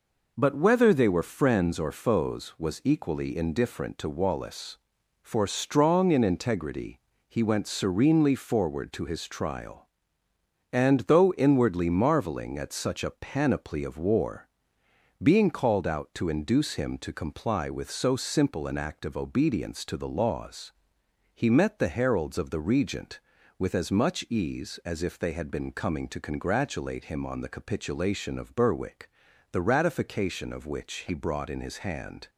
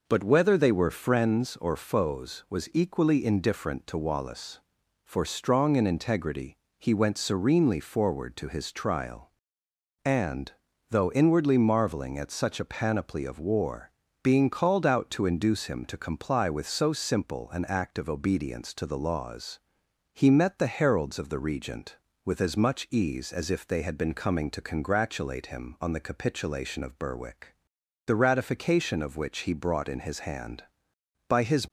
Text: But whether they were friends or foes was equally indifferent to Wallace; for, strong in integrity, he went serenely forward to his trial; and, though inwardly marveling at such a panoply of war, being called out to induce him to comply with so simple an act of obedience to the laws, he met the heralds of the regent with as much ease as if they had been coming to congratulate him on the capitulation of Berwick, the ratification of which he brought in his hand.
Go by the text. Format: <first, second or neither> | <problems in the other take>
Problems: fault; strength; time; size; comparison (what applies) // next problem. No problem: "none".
first | goes on to say "By his"; slight; from 31.2 s on; 0.40 s long